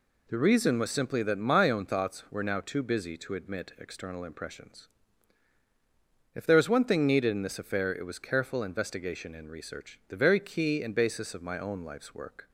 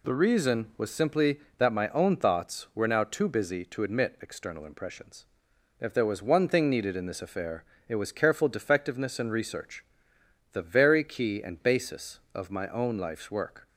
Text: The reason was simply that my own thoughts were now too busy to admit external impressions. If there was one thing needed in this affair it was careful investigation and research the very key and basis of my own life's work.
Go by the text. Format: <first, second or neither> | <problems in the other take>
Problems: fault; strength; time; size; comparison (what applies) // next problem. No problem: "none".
first | pauses between "affair" and "it"; slight; at 7.6 s; 0.24 s long // says "defectiveness" for "investigation"; at 8.4 s // pauses between "research" and "the"; noticeable; at 9.8 s; 0.68 s long